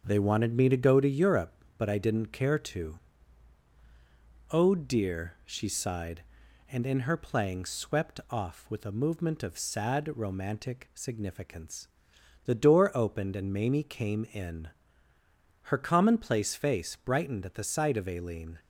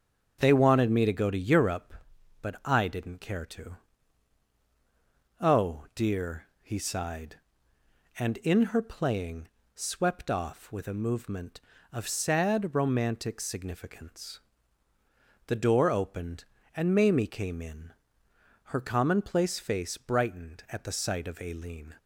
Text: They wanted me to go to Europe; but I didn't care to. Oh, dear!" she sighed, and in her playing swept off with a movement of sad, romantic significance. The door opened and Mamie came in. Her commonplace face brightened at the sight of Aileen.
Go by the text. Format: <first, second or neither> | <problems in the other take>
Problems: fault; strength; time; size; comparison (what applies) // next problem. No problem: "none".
first | starts louder than the rest; strong; until 1.4 s; 8.5 dB; also in the first // says "he" for "she"; at 6.6 s // pauses between "playing" and "swept"; slight; at 9.4 s; 0.26 s long